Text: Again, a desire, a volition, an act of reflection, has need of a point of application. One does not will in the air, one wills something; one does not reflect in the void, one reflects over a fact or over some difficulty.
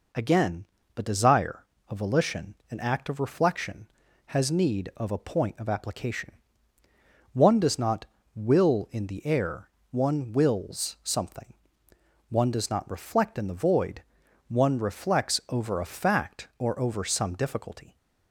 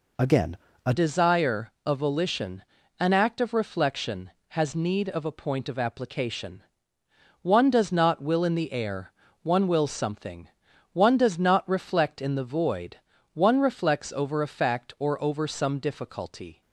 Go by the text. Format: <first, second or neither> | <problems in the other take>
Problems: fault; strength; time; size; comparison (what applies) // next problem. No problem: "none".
first | changes voice at "desire"; from 0.9 s on; 15.7 s long